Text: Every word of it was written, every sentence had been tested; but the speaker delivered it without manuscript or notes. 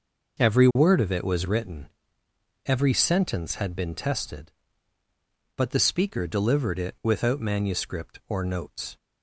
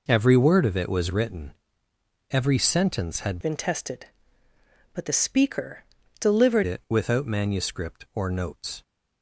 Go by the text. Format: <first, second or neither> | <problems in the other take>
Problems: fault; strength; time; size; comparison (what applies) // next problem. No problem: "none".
first | changes voice from "been" to "delivered"; from 3.4 to 6.6 s; 3.2 s long // pauses between "speaker" and "delivered"; slight; at 5.8 s; 0.36 s long